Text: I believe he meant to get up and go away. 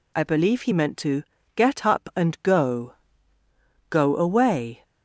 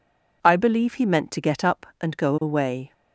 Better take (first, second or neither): second